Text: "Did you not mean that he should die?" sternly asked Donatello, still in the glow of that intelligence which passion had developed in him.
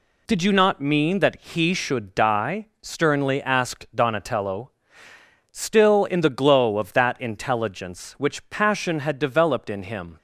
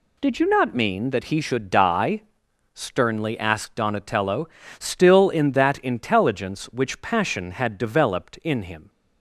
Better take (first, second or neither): first